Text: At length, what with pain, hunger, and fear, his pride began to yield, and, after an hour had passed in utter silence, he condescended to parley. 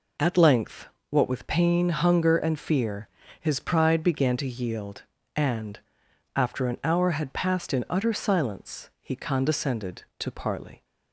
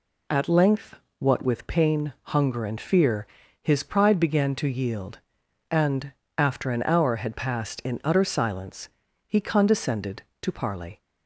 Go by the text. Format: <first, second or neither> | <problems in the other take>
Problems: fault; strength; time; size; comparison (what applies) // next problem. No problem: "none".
neither | none